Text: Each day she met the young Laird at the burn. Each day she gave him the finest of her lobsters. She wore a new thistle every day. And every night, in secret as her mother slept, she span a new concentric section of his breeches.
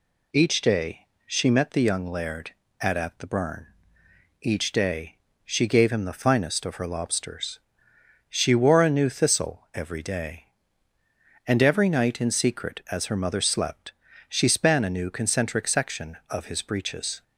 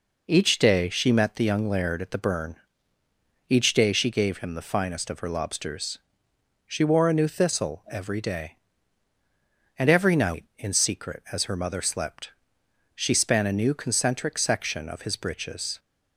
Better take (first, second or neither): second